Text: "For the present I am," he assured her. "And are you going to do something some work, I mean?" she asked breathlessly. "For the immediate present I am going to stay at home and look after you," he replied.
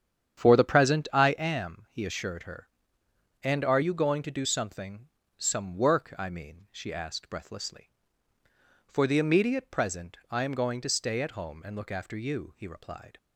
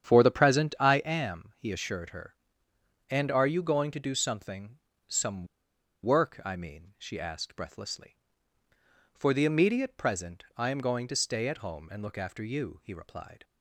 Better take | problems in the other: first | starts louder than the rest; strong; until 1.0 s; 9 dB; strong in the first // pauses between "something" and "some"; slight; at 4.7 s; 0.30 s long; slight in the first // pauses between "some" and "work"; noticeable; at 5.4 s; 0.56 s long

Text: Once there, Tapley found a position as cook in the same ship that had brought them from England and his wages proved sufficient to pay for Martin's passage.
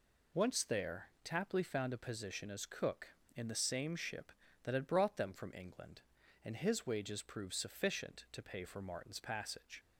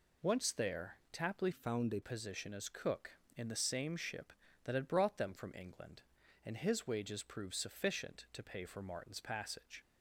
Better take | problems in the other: first | changes voice from "found" to "a"; from 1.5 to 2.0 s; 0.5 s long

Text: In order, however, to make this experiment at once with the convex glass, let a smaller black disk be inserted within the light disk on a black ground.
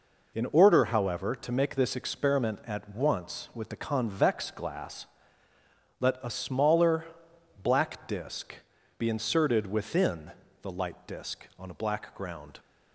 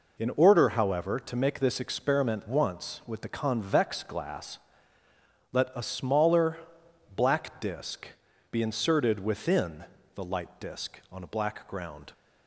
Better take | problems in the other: first | skips "at"; at 2.4 s // pauses between "smaller" and "black"; noticeable; at 6.5 s; 0.58 s long; noticeable in the first // pauses between "disk" and "be"; at 8.0 s; 0.42 s long; also in the first // pauses between "within" and "the"; slight; at 9.8 s; 0.30 s long; slight in the first

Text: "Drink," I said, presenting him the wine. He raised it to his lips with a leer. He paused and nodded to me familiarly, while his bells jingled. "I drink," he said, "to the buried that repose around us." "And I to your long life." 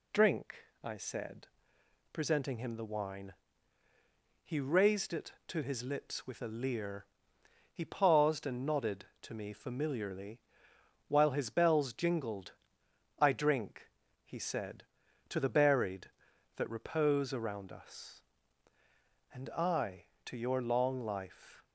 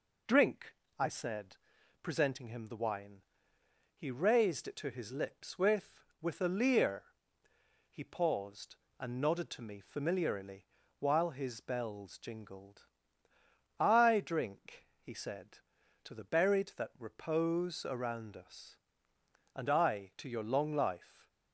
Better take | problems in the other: first | says "with" twice; at 6.2 s

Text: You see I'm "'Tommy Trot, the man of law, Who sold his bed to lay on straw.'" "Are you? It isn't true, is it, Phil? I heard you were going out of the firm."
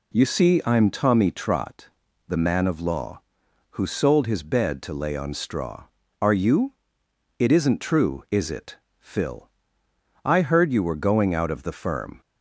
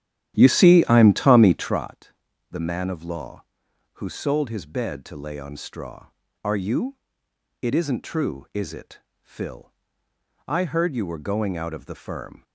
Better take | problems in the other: first | starts louder than the rest; strong; until 1.8 s; 11.5 dB

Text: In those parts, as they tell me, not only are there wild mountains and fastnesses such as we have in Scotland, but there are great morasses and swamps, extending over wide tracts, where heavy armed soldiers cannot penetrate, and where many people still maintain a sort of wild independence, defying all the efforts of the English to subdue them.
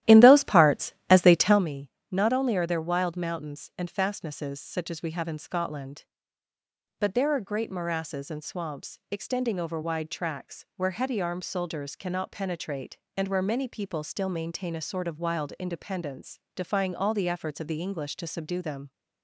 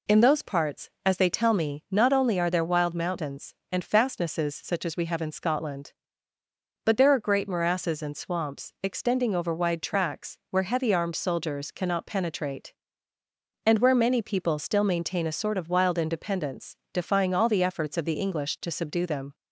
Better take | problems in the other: second | starts louder than the rest; strong; until 1.6 s; 13.5 dB

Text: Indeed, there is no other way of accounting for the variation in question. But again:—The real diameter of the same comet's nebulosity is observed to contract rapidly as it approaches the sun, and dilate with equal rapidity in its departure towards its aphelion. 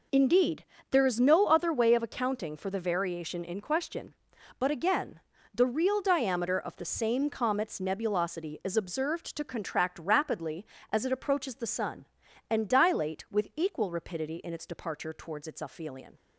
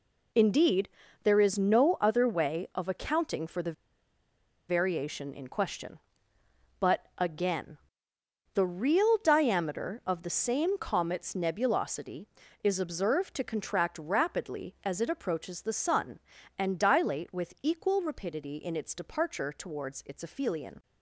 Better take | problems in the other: first | pauses between "the" and "variation"; noticeable; at 3.7 s; 0.96 s long

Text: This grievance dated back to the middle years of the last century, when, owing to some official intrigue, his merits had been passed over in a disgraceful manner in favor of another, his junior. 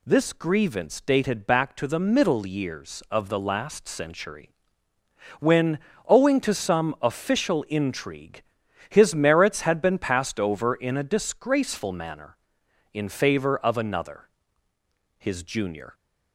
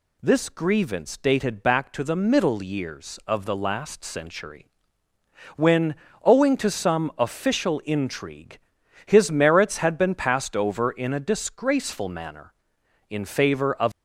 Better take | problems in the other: first | stops before "another his junior"; at 13.9 s

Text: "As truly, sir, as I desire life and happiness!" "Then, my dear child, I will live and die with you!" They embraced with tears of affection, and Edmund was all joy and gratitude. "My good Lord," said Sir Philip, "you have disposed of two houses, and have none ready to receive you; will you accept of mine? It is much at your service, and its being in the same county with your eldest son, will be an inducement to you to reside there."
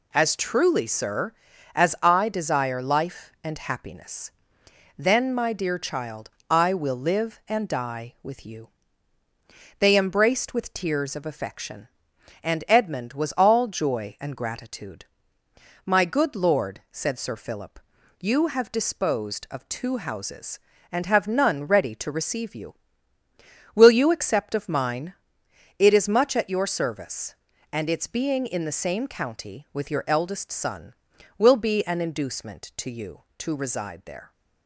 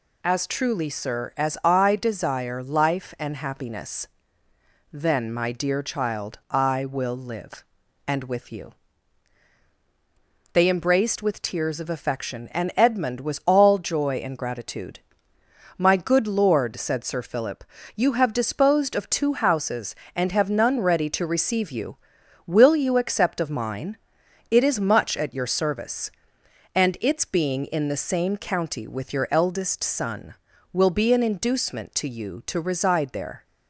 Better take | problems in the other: first | skips "die"; at 8.2 s

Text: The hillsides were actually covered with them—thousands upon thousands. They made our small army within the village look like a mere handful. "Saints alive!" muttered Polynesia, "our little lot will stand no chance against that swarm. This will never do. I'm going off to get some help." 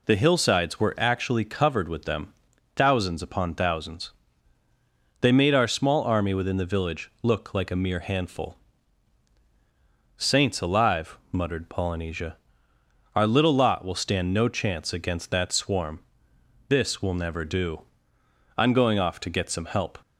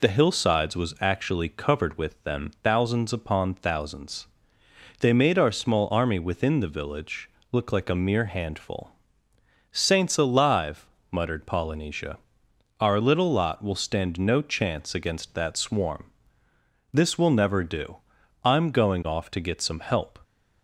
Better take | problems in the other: first | says "was" for "were"; at 0.7 s // pauses between "village" and "look"; slight; at 7.2 s; 0.22 s long

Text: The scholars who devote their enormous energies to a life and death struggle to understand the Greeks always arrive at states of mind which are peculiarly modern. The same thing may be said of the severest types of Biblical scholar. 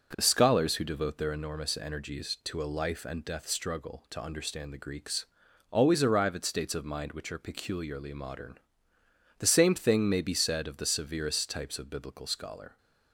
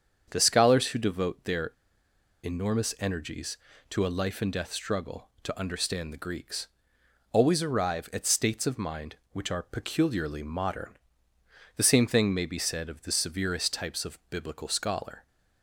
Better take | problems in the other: first | starts louder than the rest; strong; until 1.3 s; 7.5 dB // pauses between "their" and "enormous"; noticeable; at 1.7 s; 0.72 s long // pauses between "Greeks" and "always"; noticeable; at 6.6 s; 0.64 s long; noticeable in the first

